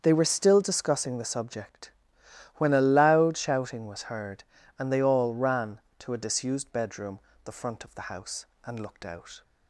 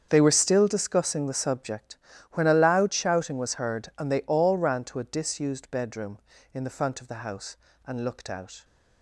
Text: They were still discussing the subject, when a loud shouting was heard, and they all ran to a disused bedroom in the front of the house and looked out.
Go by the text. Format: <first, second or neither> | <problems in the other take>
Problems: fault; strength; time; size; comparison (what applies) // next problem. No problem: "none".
second | starts louder than the rest; strong; until 1.0 s; 7.5 dB; strong in the second // skips "in"; at 7.3 s